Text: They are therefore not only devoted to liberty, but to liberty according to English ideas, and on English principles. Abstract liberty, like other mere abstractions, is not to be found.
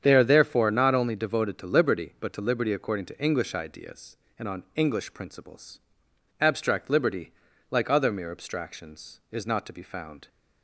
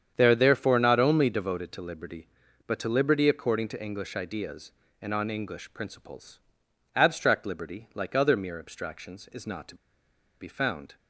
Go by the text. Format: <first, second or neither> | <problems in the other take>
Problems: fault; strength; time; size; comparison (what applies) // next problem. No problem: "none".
first | starts louder than the rest; strong; until 1.1 s; 8 dB; strong in the first // pauses between "to" and "be"; noticeable; at 9.7 s; 0.65 s long